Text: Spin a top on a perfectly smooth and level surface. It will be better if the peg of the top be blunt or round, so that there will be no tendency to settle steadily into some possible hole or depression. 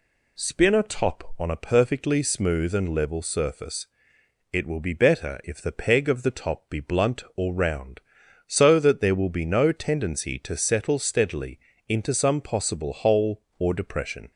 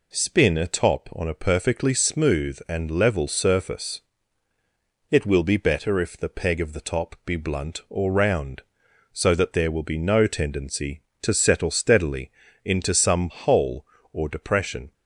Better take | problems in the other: first | pauses between "steadily" and "into"; slight; at 12.2 s; 0.36 s long; slight in the first // skips "possible"; at 13.3 s

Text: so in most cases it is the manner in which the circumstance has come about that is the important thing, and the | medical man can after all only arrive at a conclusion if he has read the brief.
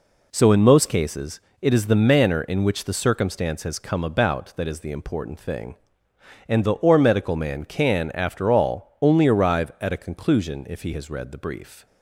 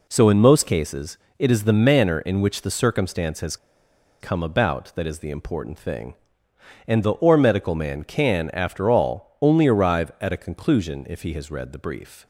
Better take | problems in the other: first | pauses between "cases" and "it"; slight; at 1.1 s; 0.20 s long; slight in the first // pauses between "has" and "come"; noticeable; at 3.5 s; 0.63 s long

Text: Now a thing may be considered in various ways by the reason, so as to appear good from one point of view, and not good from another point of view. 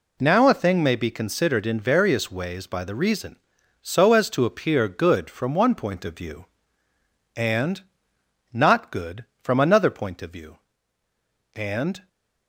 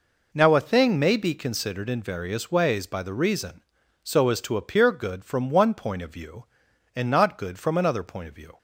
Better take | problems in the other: second | pauses between "and" and "not"; noticeable; at 7.8 s; 0.70 s long // goes on to say "And"; from 11.5 s on; 0.54 s long

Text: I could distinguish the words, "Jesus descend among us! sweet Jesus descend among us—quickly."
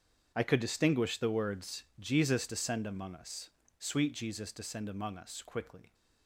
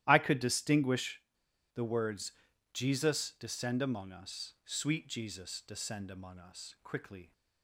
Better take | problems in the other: first | starts louder than the rest; strong; until 1.0 s; 13 dB; strong in the first // pauses between "distinguish" and "the"; noticeable; at 1.2 s; 0.52 s long

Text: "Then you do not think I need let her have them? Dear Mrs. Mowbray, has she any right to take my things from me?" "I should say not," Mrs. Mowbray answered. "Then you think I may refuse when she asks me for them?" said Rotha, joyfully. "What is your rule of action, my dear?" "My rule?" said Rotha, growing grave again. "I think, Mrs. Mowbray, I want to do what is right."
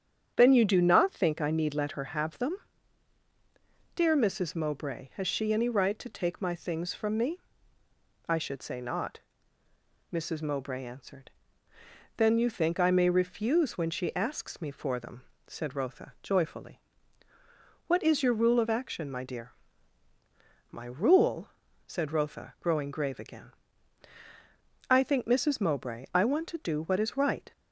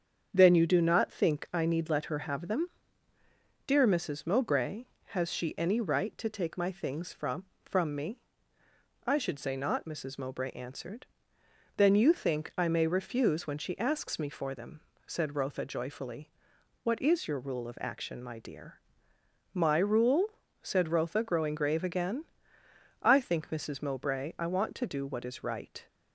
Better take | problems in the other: first | starts louder than the rest; strong; until 1.3 s; 7.5 dB; strong in the first // says "from" twice; at 7.6 s

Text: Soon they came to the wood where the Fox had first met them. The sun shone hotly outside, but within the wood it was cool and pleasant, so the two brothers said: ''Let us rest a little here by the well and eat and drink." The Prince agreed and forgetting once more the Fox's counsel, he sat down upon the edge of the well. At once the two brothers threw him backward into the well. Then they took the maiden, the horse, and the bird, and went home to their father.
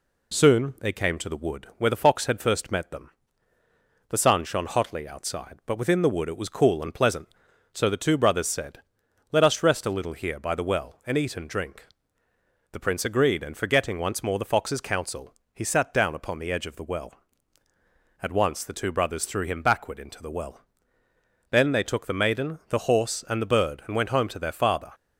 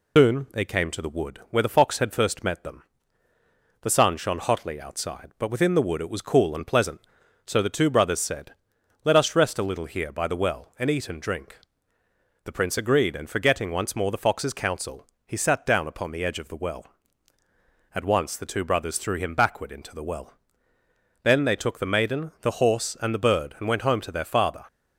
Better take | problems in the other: first | loses the start of "Soon"; at 0.1 s; 120 ms

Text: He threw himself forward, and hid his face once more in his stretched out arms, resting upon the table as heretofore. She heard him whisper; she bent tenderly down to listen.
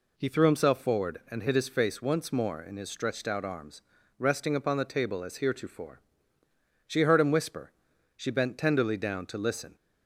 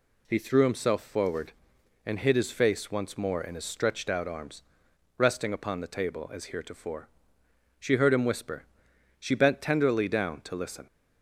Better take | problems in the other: neither | none

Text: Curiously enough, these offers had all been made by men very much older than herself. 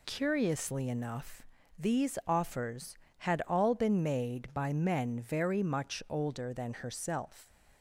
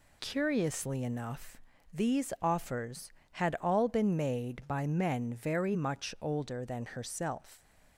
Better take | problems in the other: neither | none

